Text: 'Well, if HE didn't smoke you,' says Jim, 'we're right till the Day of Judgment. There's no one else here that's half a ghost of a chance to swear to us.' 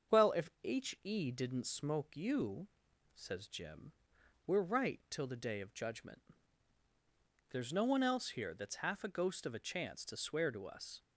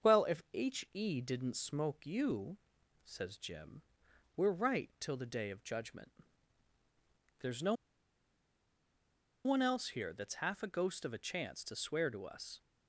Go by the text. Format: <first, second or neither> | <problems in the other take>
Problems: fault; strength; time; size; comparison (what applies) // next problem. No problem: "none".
first | starts louder than the rest; until 1.2 s; 6.5 dB; also in the first // pauses between "no" and "one"; strong; at 7.7 s; 1.7 s long